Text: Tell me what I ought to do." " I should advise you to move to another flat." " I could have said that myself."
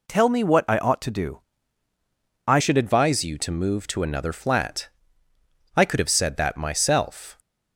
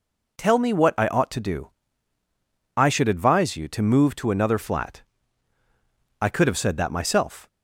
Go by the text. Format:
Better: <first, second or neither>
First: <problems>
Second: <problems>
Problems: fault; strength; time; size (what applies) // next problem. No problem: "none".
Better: second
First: changes voice at "should"; from 2.6 s on; 4.7 s long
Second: none